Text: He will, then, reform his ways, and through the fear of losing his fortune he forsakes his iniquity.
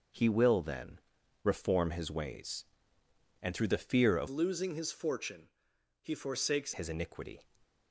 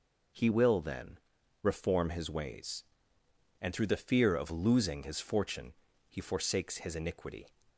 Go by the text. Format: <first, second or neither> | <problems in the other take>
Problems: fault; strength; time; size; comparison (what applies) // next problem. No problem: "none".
second | changes voice from "losing" to "forsakes"; from 4.2 to 6.7 s; 2.5 s long // pauses between "fortune" and "he"; noticeable; at 5.4 s; 0.52 s long; slight in the second